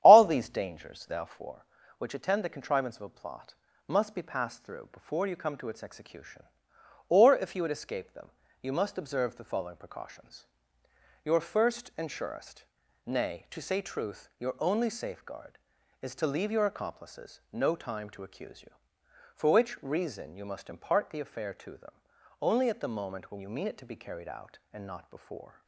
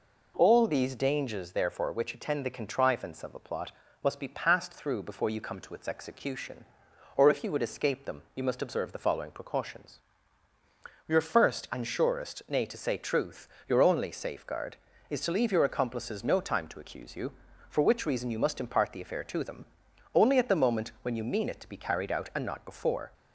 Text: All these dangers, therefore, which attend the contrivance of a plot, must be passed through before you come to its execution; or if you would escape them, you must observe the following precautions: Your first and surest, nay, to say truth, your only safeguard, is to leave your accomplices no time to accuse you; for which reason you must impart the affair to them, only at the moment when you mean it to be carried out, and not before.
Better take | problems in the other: second | starts louder than the rest; strong; until 1.5 s; 10.5 dB

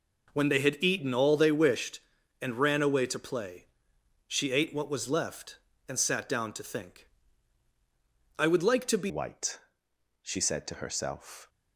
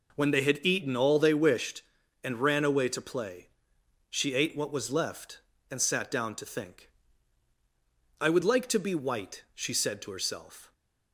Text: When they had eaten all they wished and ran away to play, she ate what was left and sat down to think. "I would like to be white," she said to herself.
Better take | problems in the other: second | changes voice at "white"; from 9.0 s on; 2.4 s long

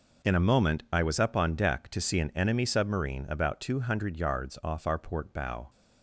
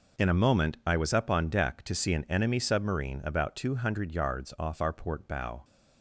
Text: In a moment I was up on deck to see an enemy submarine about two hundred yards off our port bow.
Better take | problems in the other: neither | none

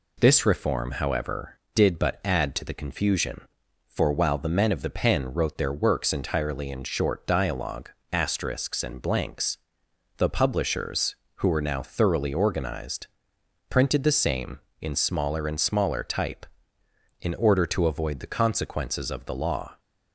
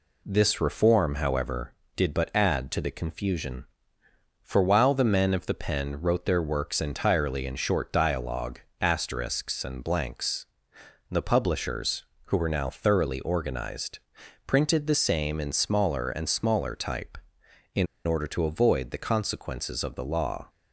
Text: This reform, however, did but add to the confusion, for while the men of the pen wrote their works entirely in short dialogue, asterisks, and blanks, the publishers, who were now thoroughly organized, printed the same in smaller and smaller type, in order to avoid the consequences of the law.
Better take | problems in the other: first | pauses between "in" and "order"; slight; at 17.8 s; 0.21 s long

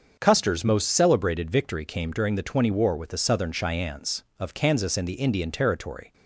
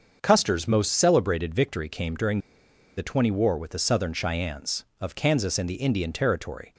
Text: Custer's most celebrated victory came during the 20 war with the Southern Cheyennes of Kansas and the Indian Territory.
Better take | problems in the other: first | starts louder than the rest; until 1.2 s; 6.5 dB; also in the first // pauses between "during" and "the"; noticeable; at 2.3 s; 0.57 s long

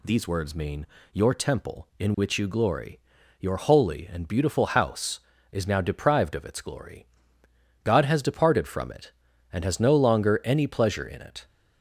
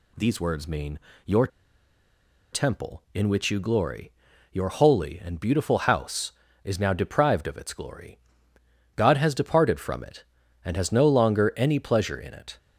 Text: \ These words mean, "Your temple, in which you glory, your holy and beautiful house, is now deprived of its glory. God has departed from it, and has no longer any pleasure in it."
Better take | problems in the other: first | pauses between "Your" and "temple"; at 1.4 s; 1.0 s long

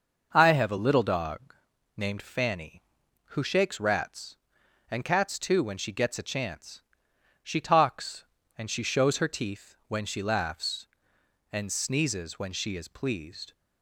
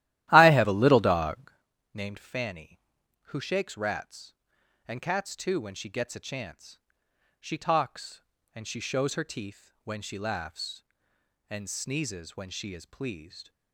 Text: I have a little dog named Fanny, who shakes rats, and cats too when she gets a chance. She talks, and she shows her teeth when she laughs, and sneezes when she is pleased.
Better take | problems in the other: first | starts louder than the rest; strong; until 1.7 s; 14 dB // pauses between "dog" and "named"; at 1.5 s; 0.42 s long; also in the first

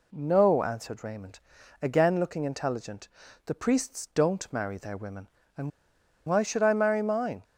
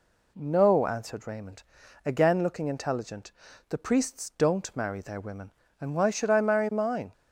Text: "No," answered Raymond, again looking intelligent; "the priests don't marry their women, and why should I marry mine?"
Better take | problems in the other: second | pauses between "and" and "why"; noticeable; at 5.7 s; 0.56 s long

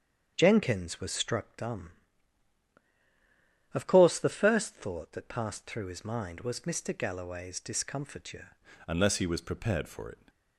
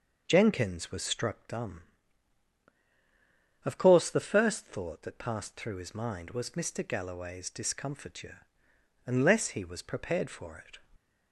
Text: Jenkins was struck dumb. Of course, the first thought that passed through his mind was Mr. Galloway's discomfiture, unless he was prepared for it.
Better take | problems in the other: second | starts louder than the rest; strong; until 1.3 s; 7.5 dB // changes voice at "unless"; from 8.8 s on; 1.4 s long

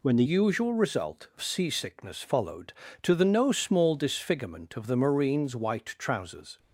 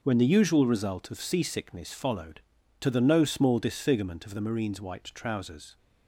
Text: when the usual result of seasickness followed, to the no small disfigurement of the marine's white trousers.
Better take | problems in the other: second | changes voice at "usual"; from 0.2 s on; 6.3 s long

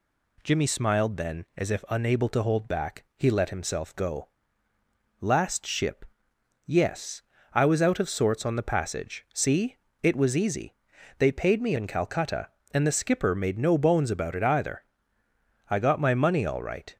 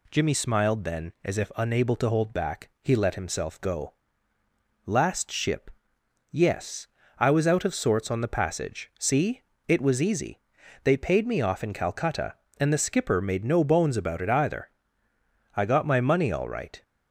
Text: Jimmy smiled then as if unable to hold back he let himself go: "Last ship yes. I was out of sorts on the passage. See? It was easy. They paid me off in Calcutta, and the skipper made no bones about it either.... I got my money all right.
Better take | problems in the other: second | pauses between "ship" and "yes"; noticeable; at 6.0 s; 0.60 s long; noticeable in the second // skips "off"; at 11.7 s

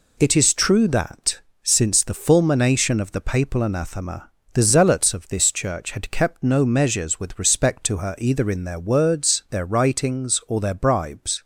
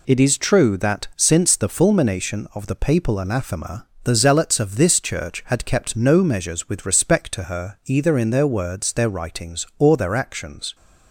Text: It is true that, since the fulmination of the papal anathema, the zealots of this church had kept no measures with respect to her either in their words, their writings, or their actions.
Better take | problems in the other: second | says "bribes" for "actions"; at 10.7 s

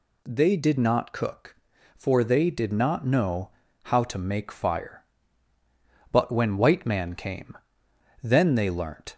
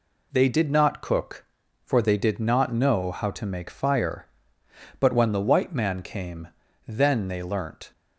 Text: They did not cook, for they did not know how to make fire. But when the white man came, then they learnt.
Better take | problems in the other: second | pauses between "know" and "how"; slight; at 3.4 s; 0.34 s long // skips "the"; at 6.5 s

